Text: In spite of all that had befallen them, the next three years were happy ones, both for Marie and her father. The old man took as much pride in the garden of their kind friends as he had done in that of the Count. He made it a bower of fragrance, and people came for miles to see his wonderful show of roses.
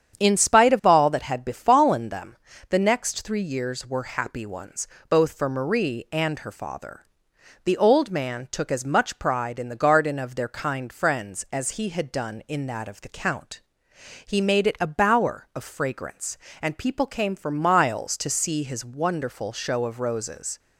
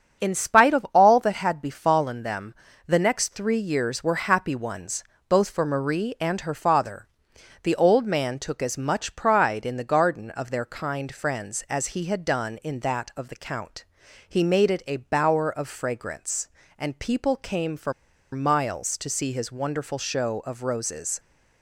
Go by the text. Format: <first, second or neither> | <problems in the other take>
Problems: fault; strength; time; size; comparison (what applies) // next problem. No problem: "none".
first | starts louder than the rest; strong; until 1.2 s; 7.5 dB; strong in the first // pauses between "for" and "miles"; at 17.9 s; 0.40 s long